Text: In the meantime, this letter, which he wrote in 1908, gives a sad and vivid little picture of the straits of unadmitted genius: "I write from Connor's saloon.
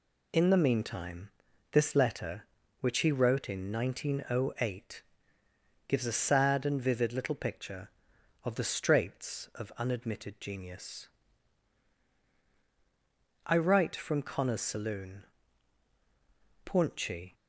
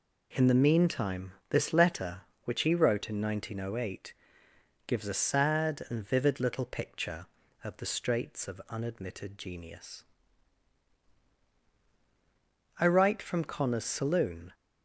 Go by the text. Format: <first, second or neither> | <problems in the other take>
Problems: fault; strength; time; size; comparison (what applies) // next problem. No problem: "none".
second | goes on to say "Paunchy"; noticeable; from 16.6 s on; 0.70 s long